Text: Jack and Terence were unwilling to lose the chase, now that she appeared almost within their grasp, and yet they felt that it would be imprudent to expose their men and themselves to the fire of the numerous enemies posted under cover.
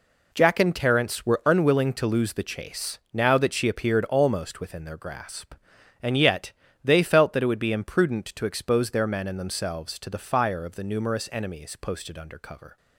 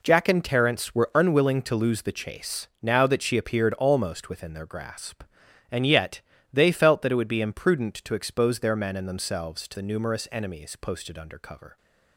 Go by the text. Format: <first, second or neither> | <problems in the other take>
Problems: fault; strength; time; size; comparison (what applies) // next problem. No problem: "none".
first | pauses between "yet" and "they"; slight; at 6.2 s; 0.30 s long; slight in the first // skips "the fire of"; at 9.7 s